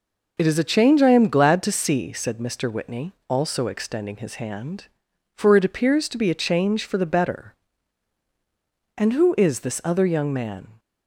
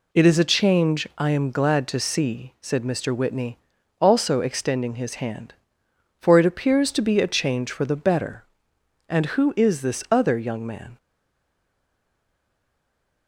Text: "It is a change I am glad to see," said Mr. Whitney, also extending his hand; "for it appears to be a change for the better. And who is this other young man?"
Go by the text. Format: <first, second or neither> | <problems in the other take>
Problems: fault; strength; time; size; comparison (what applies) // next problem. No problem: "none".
first | stays silent after the last word; from 10.9 s on; 2.3 s long